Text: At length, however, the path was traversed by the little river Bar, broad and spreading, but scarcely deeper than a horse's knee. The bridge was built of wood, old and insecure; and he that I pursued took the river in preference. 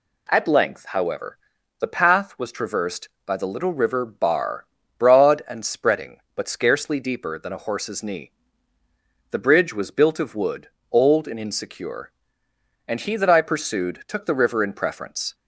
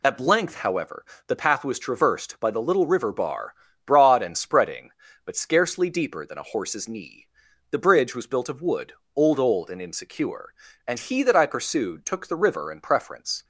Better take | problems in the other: first | says "old" twice; at 9.3 s

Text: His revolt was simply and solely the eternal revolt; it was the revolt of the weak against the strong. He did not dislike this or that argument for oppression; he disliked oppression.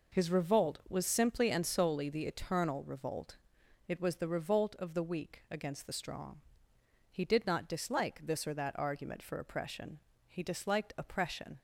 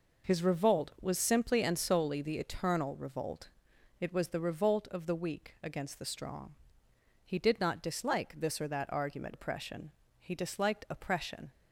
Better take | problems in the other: first | skips "for"; at 9.3 s

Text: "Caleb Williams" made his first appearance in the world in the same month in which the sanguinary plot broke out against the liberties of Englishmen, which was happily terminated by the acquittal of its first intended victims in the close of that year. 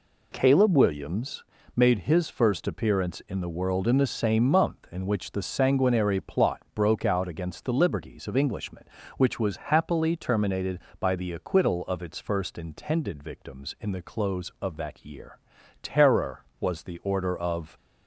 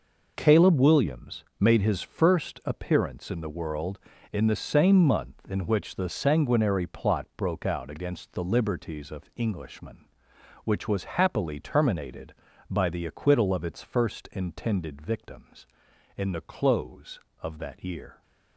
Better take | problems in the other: second | pauses between "Williams" and "made"; slight; at 1.4 s; 0.32 s long; slight in the second // goes on to say "Terror was the order of"; strong; from 15.8 s on; 1.9 s long

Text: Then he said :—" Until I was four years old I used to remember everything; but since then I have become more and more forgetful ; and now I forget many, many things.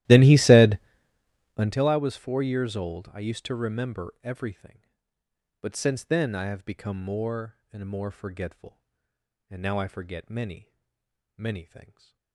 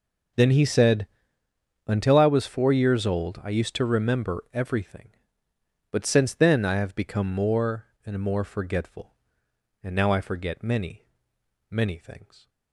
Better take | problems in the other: second | starts louder than the rest; strong; until 1.8 s; 14 dB // stays silent after the last word; slight; from 11.8 s on; 0.5 s long

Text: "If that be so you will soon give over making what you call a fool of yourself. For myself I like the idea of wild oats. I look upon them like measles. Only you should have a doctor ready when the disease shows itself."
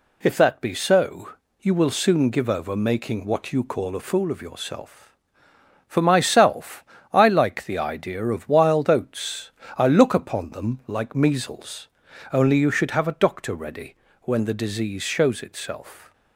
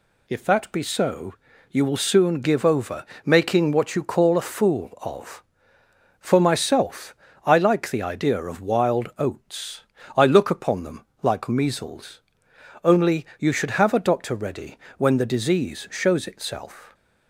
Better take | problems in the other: first | pauses between "so" and "you"; slight; at 1.3 s; 0.36 s long; slight in the first // pauses between "over" and "making"; slight; at 3.0 s; 0.18 s long // skips "yourself"; at 5.8 s // pauses between "myself" and "I"; slight; at 7.1 s; 0.30 s long; slight in the first // pauses between "them" and "like"; slight; at 11.0 s; 0.16 s long // pauses between "ready" and "when"; slight; at 14.7 s; 0.20 s long; slight in the first

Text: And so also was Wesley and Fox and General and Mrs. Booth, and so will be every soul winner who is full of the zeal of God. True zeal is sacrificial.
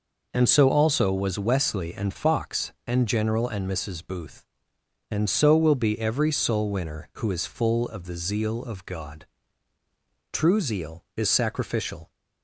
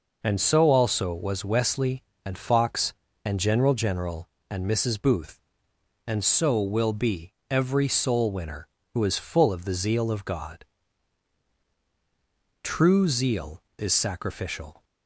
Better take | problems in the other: first | says "General" twice; at 3.7 s // pauses between "be" and "every"; slight; at 7.3 s; 0.16 s long

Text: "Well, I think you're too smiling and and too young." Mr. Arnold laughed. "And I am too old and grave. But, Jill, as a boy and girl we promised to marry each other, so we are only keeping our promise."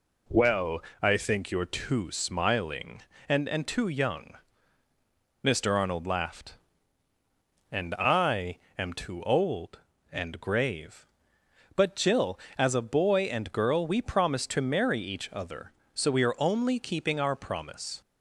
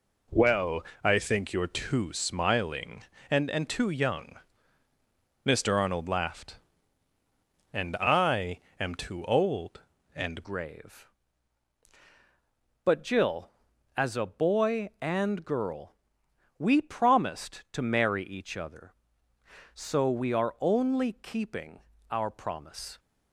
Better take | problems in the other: first | pauses between "I" and "am"; slight; at 8.5 s; 0.18 s long; slight in the first // changes voice at "grave"; from 10.4 s on; 12.5 s long // pauses between "girl" and "we"; noticeable; at 15.9 s; 0.66 s long // pauses between "keeping" and "our"; slight; at 21.8 s; 0.30 s long

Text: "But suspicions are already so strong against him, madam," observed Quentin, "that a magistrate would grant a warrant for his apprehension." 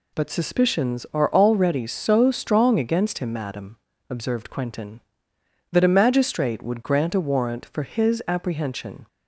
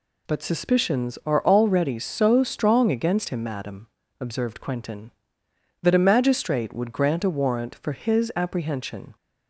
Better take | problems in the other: neither | none

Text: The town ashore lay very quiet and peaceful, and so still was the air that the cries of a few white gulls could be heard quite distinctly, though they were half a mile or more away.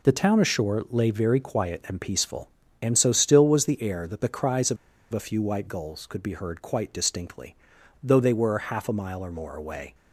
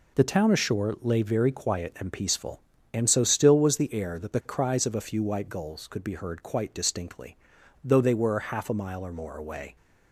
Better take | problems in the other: second | pauses between "of" and "a"; slight; at 4.7 s; 0.35 s long

